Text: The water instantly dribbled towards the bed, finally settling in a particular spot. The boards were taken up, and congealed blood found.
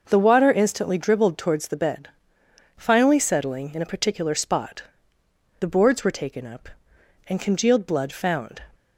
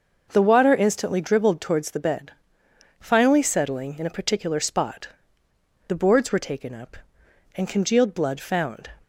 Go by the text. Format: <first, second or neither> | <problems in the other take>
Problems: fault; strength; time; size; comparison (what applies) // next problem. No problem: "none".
neither | none